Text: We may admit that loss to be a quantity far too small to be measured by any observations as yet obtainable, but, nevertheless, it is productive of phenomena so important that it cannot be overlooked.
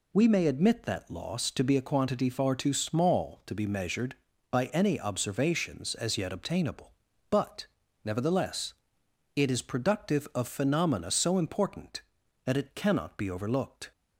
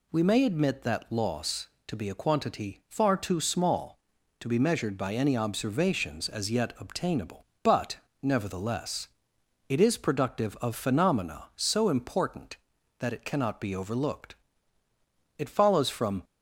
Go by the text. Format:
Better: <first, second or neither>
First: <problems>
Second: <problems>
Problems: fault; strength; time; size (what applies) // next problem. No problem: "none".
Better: first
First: none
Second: goes on to say "It follows from"; noticeable; from 15.3 s on; 0.86 s long